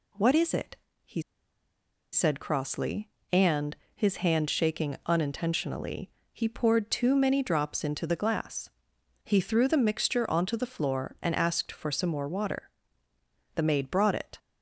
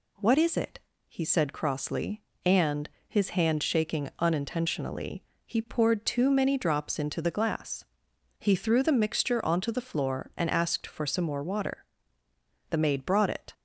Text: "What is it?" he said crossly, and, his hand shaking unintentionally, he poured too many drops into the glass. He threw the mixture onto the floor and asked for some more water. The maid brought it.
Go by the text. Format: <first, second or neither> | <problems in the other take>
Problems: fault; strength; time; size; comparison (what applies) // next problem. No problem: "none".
second | pauses between "he" and "said"; noticeable; at 1.2 s; 0.90 s long